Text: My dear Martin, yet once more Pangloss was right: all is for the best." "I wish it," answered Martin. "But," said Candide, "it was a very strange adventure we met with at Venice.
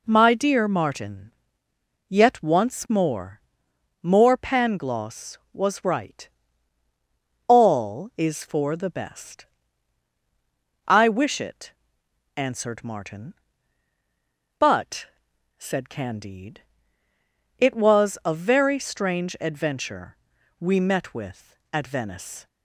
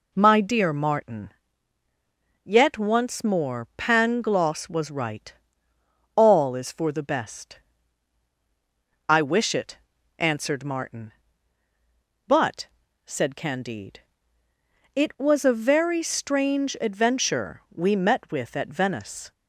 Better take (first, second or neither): second